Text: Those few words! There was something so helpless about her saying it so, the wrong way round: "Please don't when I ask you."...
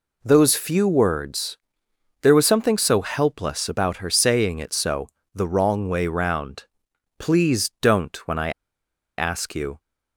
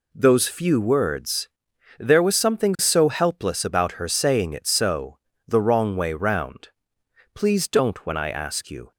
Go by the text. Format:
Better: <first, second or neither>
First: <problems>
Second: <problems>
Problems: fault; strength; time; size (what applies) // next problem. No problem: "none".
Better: second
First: pauses between "I" and "ask"; noticeable; at 8.5 s; 0.67 s long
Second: none